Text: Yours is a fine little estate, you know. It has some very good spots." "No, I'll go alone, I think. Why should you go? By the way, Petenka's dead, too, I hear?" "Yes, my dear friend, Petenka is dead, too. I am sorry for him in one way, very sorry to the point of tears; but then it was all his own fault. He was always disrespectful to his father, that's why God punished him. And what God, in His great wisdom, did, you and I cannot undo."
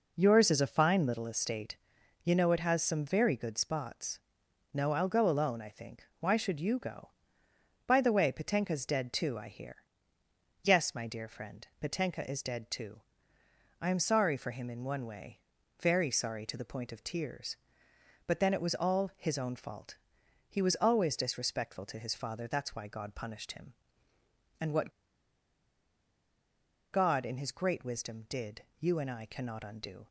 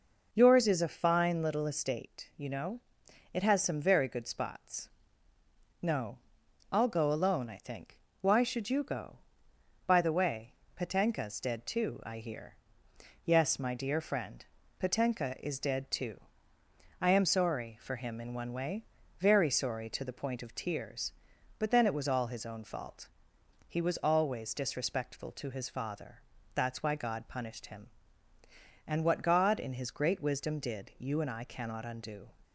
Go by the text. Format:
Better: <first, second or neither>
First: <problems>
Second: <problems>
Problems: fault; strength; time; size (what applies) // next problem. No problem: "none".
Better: second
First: pauses between "what" and "God"; strong; at 24.9 s; 2.0 s long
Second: none